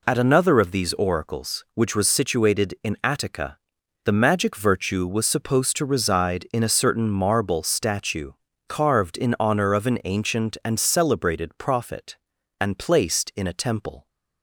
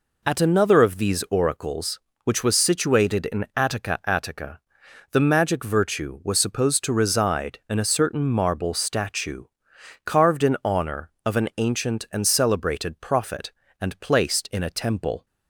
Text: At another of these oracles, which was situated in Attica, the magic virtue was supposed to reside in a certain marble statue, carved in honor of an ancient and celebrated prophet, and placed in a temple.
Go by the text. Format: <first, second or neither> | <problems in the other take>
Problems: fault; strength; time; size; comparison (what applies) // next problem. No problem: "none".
first | says "Attica" twice; at 4.0 s